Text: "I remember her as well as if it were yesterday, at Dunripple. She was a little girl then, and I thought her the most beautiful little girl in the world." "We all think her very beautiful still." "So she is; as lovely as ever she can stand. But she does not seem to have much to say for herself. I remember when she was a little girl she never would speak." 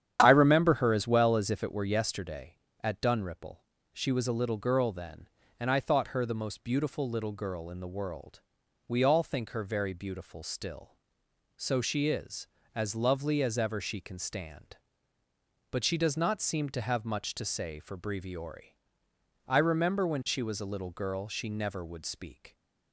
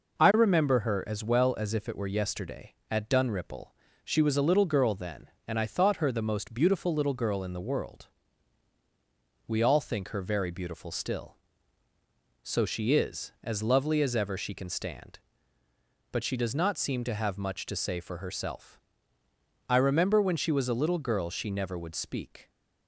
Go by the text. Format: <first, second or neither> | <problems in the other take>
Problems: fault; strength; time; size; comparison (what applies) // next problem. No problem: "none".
second | starts louder than the rest; strong; until 1.2 s; 9.5 dB // says "breviori" for "herself"; at 17.9 s